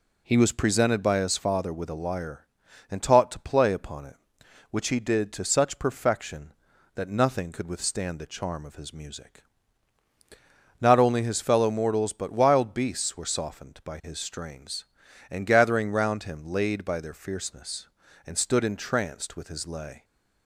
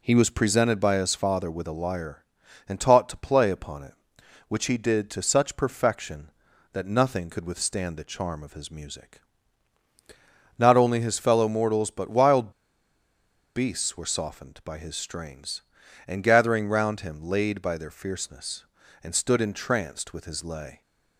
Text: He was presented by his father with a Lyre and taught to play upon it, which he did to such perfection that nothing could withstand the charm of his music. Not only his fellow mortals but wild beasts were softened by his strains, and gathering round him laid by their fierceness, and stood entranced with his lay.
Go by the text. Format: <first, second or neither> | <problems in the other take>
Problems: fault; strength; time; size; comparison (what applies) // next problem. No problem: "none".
first | pauses between "wild" and "beasts"; at 12.5 s; 1.0 s long